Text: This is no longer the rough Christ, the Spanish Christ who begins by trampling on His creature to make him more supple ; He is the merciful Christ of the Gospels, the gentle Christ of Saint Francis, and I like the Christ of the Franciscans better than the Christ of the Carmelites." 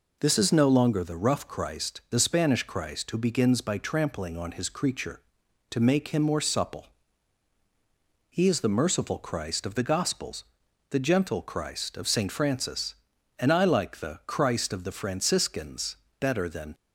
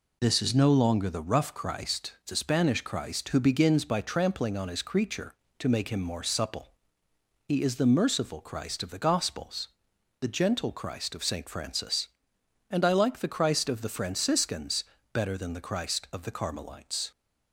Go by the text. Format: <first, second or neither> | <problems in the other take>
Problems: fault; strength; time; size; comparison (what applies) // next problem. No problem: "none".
second | pauses between "Franciscans" and "better"; slight; at 15.9 s; 0.24 s long; slight in the second // stops before "the Christ of the Carmelites"; at 16.7 s